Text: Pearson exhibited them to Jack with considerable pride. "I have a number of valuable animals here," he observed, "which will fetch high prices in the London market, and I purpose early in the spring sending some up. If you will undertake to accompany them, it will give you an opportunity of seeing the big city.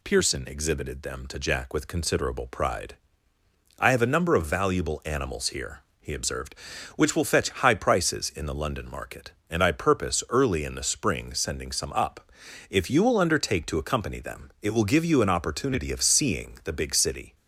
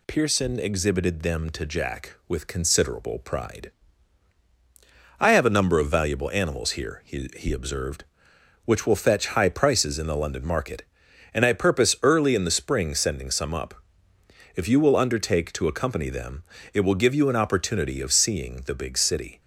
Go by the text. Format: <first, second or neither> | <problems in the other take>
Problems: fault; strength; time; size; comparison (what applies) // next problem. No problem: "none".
first | says "he" twice; at 7.3 s